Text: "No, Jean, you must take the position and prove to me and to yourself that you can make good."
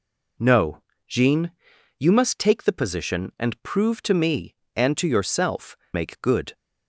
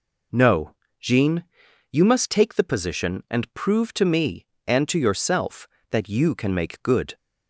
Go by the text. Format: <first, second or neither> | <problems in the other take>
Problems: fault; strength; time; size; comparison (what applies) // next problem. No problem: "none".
second | skips "that you can"; at 5.8 s